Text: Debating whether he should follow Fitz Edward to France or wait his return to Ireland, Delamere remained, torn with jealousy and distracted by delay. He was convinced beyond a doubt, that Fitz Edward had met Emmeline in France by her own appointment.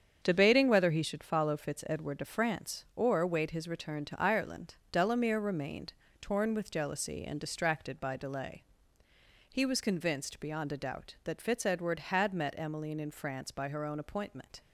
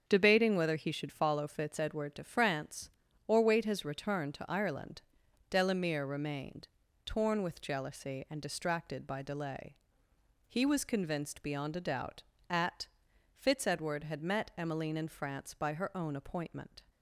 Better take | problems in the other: first | starts louder than the rest; strong; until 1.0 s; 7 dB; strong in the first // says "at" for "that"; at 12.4 s

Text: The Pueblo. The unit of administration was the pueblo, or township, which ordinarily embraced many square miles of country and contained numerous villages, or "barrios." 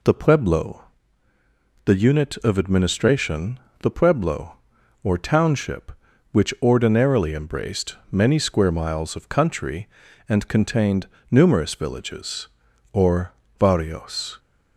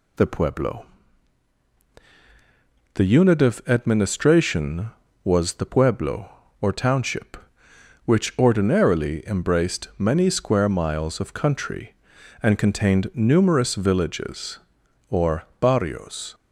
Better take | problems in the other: second | skips "was"; at 3.6 s // pauses between "contained" and "numerous"; slight; at 11.0 s; 0.24 s long // pauses between "or" and "barrios"; slight; at 13.3 s; 0.26 s long; slight in the second

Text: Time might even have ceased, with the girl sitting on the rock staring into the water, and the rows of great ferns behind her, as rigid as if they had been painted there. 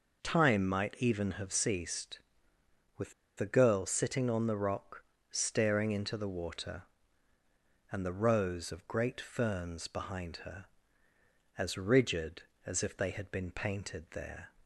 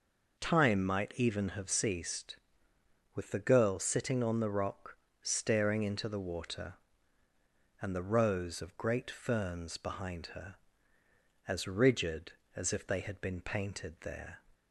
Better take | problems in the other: second | pauses between "with" and "the"; slight; at 3.1 s; 0.25 s long // pauses between "rock" and "staring"; slight; at 5.0 s; 0.28 s long; slight in the second

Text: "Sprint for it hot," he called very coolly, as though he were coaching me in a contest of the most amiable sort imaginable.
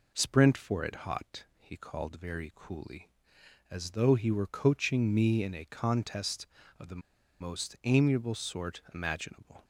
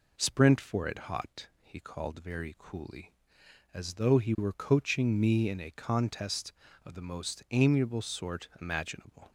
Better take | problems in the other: second | pauses between "the" and "most"; at 7.0 s; 0.39 s long

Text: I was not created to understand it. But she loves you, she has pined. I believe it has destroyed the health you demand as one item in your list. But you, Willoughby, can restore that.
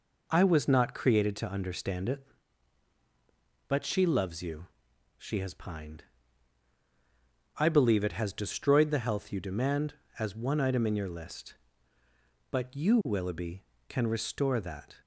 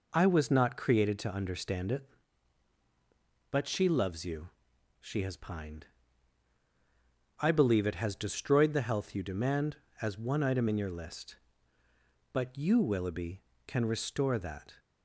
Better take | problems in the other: neither | none

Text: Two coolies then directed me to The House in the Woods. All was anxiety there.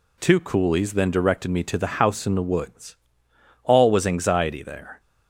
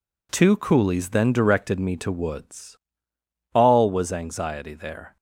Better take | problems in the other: first | skips "The House in the"; at 2.1 s

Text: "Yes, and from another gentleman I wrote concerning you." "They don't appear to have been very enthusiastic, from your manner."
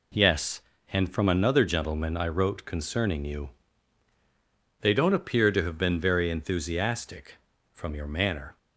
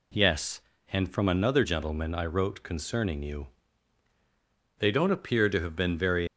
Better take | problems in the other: first | stops before "enthusiastic from your manner"; at 6.2 s

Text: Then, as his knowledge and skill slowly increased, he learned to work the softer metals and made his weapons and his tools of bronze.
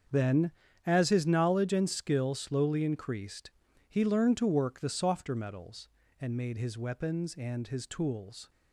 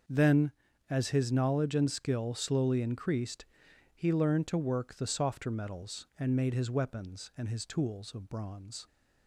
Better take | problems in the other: second | starts louder than the rest; strong; until 1.4 s; 7 dB; also in the second // stops before "of bronze"; at 8.4 s

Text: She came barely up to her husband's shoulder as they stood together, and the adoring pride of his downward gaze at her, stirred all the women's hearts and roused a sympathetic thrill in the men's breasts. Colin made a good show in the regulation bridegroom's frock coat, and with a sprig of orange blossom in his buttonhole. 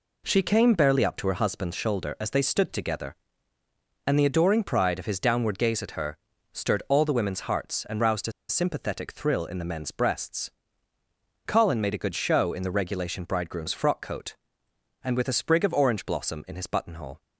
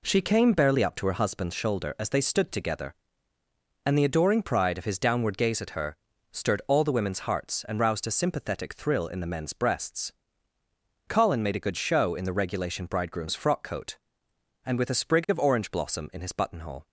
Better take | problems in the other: second | pauses between "a" and "sympathetic"; slight; at 8.3 s; 0.18 s long

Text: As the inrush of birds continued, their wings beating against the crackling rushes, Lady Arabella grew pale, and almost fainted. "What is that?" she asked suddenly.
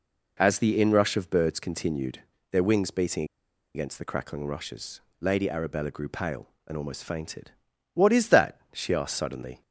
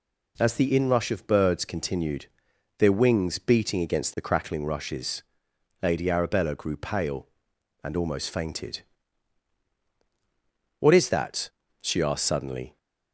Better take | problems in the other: second | pauses between "beating" and "against"; noticeable; at 3.2 s; 0.50 s long

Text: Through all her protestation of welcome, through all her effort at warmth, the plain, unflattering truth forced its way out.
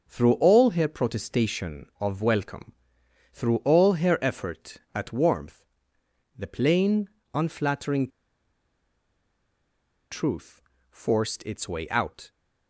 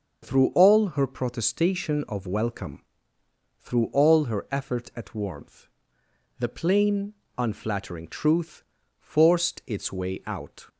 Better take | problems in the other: second | starts louder than the rest; noticeable; until 1.1 s; 6 dB; also in the second // pauses between "unflattering" and "truth"; strong; at 8.0 s; 2.0 s long // pauses between "truth" and "forced"; slight; at 10.6 s; 0.28 s long; slight in the second

